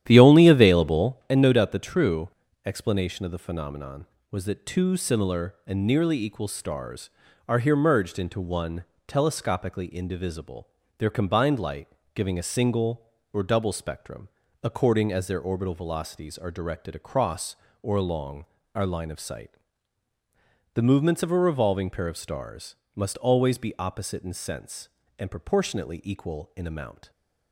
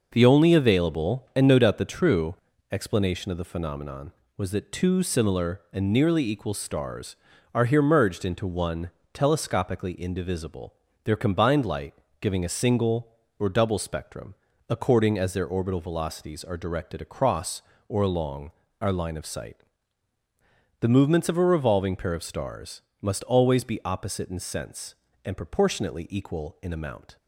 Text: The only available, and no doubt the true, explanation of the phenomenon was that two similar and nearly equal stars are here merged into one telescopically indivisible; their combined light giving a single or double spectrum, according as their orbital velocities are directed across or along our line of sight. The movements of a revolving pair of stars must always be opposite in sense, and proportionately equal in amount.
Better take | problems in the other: second | starts louder than the rest; strong; until 1.1 s; 11 dB // pauses between "one" and "telescopically"; slight; at 8.8 s; 0.24 s long; slight in the second // pauses between "light" and "giving"; slight; at 11.8 s; 0.26 s long; slight in the second // pauses between "along" and "our"; slight; at 18.4 s; 0.32 s long; slight in the second // pauses between "stars" and "must"; slight; at 22.7 s; 0.18 s long; slight in the second

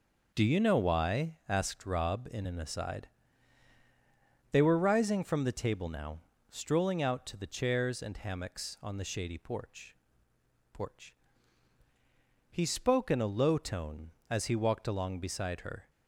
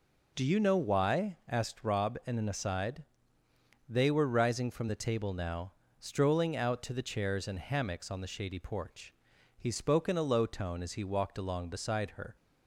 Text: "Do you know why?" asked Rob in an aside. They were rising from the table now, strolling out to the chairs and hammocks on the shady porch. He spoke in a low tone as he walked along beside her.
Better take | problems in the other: second | starts louder than the rest; noticeable; until 1.4 s; 6 dB // says "porch" twice; at 10.7 s

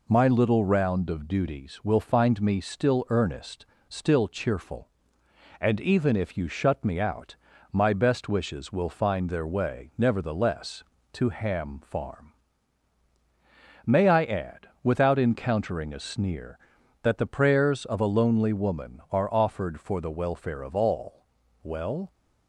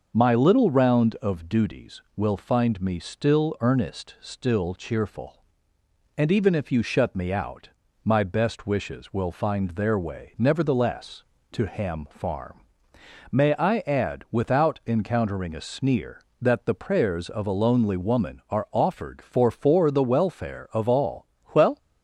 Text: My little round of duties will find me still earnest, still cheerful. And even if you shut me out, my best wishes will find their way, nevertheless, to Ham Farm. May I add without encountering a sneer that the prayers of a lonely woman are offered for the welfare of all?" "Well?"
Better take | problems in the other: first | starts louder than the rest; until 1.1 s; 6 dB // says "for" twice; at 19.5 s

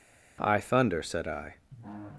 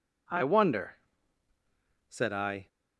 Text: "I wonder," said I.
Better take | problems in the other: second | says "thunder" for "wonder"; at 0.6 s

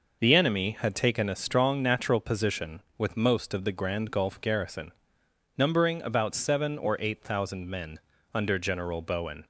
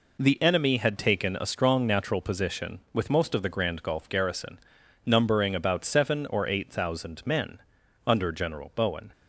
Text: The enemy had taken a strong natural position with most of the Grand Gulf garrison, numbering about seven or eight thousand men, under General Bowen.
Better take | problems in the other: neither | none

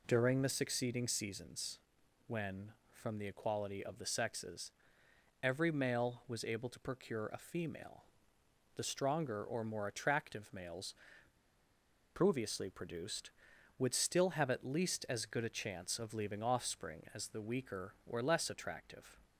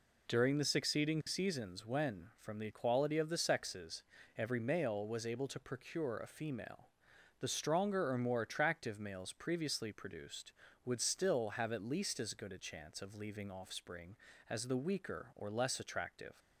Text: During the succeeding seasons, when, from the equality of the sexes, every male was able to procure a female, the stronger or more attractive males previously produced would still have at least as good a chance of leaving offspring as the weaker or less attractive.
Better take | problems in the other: second | pauses between "males" and "previously"; at 10.9 s; 1.2 s long

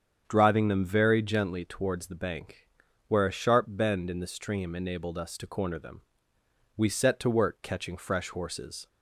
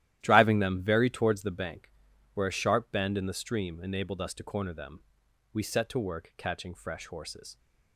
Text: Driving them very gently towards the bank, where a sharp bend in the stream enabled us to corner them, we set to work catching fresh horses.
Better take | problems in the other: first | starts louder than the rest; strong; until 1.2 s; 13 dB; strong in the first // skips "gently"; at 1.0 s

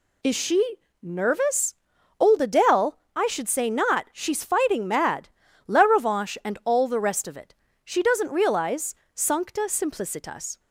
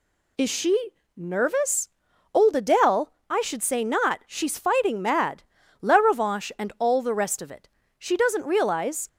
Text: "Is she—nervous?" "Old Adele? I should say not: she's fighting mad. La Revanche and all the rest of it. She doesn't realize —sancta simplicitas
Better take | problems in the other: first | stops before "sancta simplicitas"; at 9.0 s

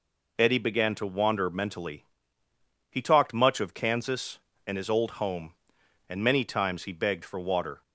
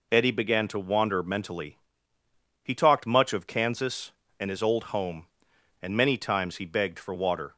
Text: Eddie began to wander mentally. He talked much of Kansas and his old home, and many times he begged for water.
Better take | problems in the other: neither | none

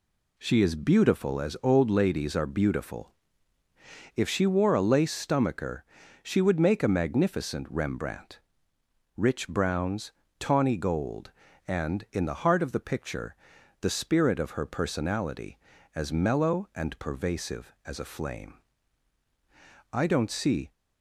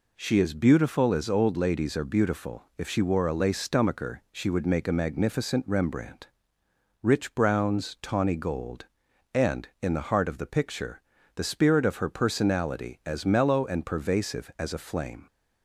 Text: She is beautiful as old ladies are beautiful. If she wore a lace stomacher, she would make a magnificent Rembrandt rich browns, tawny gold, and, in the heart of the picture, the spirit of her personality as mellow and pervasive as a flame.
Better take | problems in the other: second | pauses between "Rembrandt" and "rich"; noticeable; at 8.3 s; 0.78 s long; noticeable in the second // goes on to say "I don't see"; noticeable; from 19.9 s on; 0.78 s long

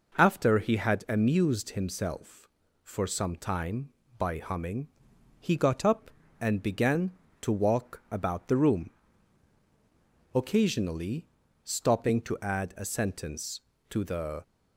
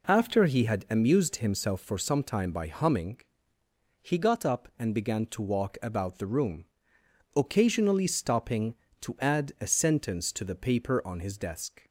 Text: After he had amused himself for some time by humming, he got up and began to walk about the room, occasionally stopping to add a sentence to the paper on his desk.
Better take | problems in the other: second | pauses between "occasionally" and "stopping"; slight; at 11.2 s; 0.36 s long // stops before "paper on his desk"; at 14.4 s

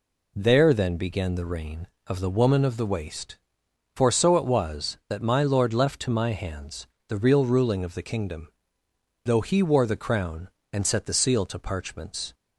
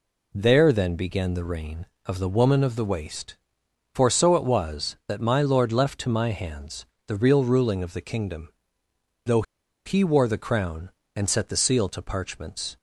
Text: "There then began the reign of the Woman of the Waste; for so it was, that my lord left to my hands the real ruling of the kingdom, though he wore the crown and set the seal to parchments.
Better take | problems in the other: first | pauses between "hands" and "the"; slight; at 6.8 s; 0.20 s long; slight in the first // pauses between "though" and "he"; at 9.4 s; 0.43 s long

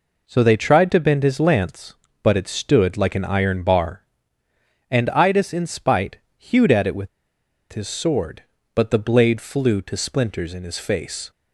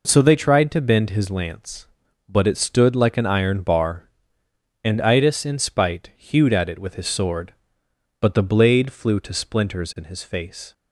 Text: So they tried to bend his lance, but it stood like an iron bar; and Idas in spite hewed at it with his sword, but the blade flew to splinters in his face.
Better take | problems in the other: second | pauses between "spite" and "hewed"; slight; at 6.1 s; 0.20 s long // pauses between "with" and "his"; noticeable; at 7.0 s; 0.63 s long

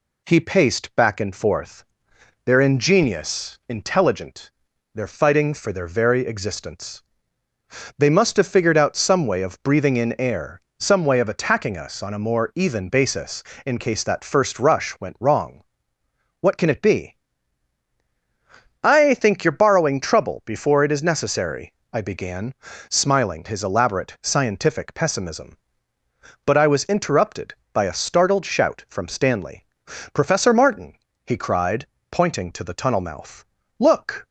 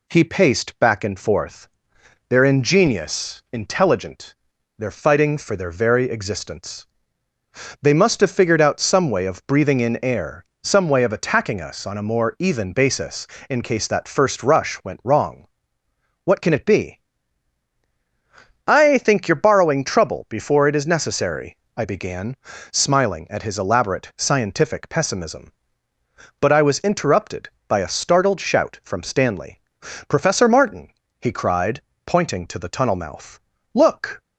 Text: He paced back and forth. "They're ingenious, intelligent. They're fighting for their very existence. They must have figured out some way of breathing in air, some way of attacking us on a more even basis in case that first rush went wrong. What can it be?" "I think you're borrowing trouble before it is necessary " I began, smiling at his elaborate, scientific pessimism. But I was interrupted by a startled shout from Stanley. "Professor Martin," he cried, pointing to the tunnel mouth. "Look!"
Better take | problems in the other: second | skips "at"; at 23.4 s

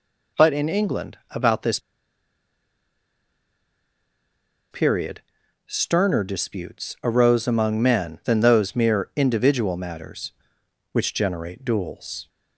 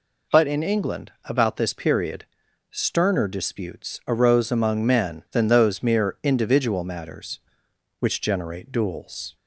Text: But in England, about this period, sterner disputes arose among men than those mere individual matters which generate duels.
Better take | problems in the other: second | pauses between "this" and "period"; strong; at 1.7 s; 2.9 s long

